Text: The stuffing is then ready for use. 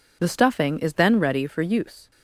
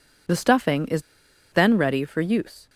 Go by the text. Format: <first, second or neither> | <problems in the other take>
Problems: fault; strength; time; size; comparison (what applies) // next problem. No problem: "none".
first | pauses between "is" and "then"; noticeable; at 1.0 s; 0.49 s long